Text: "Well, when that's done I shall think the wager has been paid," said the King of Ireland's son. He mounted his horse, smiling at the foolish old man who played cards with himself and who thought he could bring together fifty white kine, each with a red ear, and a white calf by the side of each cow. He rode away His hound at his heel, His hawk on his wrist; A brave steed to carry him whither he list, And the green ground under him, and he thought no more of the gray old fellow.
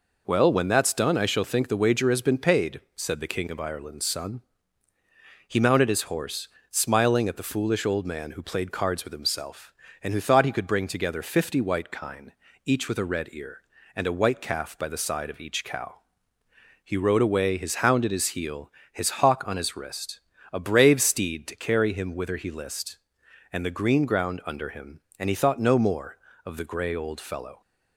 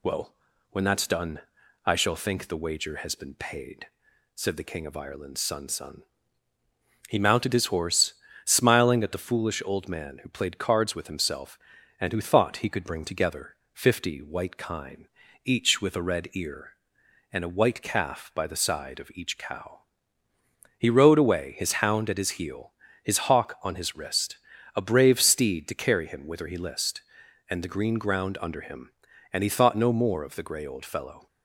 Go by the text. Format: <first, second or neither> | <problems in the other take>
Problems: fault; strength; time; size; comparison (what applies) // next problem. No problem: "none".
first | pauses between "done" and "I"; at 1.4 s; 0.44 s long // says "son" twice; at 5.6 s // pauses between "together" and "fifty"; slight; at 13.5 s; 0.16 s long